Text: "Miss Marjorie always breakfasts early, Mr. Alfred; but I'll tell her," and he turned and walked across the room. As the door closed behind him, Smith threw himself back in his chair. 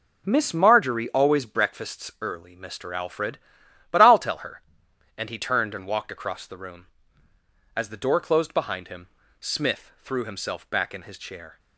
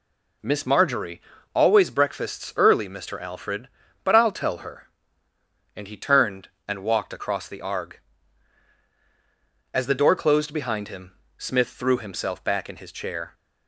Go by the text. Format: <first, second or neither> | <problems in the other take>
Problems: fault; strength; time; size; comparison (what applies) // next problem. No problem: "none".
first | pauses between "Marjorie" and "always"; slight; at 1.2 s; 0.32 s long // says "arg" for "room"; at 7.6 s